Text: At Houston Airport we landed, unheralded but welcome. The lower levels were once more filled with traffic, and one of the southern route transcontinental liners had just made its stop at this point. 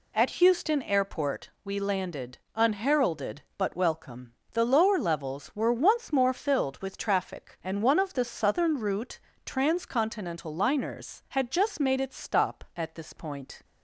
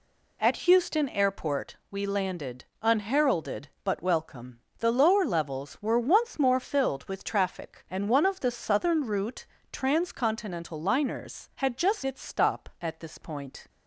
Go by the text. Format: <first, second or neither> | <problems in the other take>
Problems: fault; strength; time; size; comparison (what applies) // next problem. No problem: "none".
first | pauses between "route" and "transcontinental"; slight; at 9.4 s; 0.26 s long; slight in the first // skips "made"; at 12.0 s